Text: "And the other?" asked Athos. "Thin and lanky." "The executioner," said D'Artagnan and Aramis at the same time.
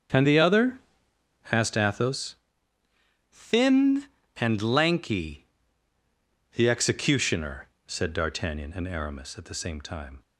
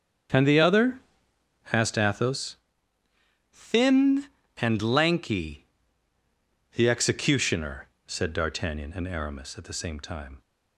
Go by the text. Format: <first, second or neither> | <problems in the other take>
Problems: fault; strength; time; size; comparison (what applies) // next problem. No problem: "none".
neither | starts louder than the rest; strong; the same in both